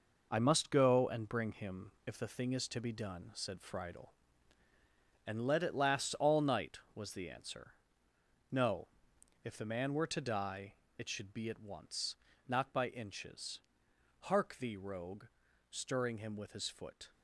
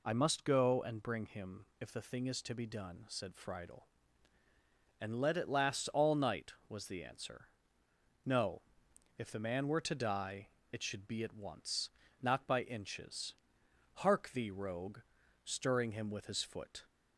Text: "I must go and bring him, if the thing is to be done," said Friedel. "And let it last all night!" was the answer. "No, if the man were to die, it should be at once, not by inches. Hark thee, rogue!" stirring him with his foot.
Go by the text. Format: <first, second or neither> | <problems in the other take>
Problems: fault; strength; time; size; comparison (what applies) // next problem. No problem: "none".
second | gets quieter; strong; throughout; 7 dB